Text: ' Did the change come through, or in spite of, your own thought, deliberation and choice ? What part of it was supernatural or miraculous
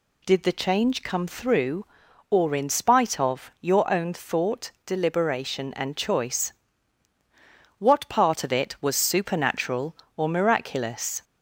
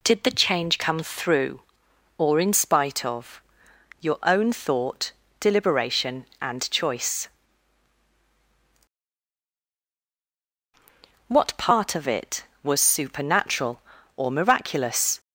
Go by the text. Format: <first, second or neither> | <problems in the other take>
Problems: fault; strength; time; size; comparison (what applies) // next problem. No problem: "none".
neither | none